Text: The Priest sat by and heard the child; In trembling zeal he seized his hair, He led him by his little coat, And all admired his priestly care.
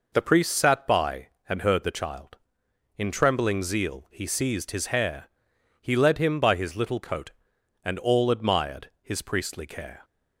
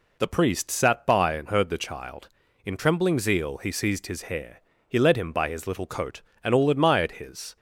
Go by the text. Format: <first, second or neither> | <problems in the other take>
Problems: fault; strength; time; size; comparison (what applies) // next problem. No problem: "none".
first | stops before "priestly care"; at 7.5 s